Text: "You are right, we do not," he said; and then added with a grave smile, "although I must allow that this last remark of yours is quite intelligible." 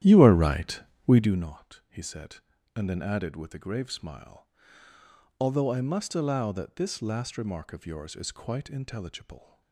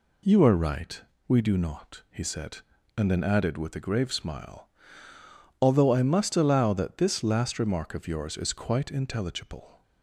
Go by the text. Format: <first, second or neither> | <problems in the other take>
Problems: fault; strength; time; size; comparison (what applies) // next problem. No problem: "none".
second | starts louder than the rest; strong; until 1.5 s; 11.5 dB